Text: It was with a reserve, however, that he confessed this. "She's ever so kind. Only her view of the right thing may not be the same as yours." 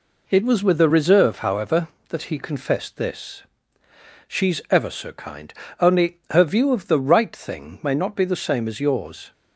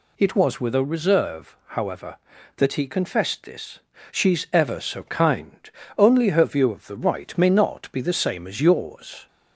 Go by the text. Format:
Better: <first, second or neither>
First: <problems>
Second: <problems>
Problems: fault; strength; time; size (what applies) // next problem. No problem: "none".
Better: first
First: none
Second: skips "thing"; at 7.3 s